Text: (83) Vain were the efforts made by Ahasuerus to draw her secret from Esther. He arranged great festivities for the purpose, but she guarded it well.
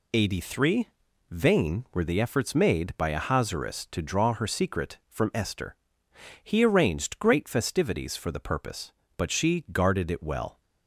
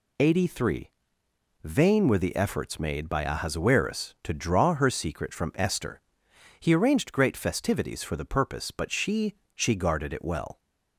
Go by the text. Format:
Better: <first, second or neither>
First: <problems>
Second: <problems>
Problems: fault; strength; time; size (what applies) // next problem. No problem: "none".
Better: first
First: none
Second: says "she" twice; at 9.5 s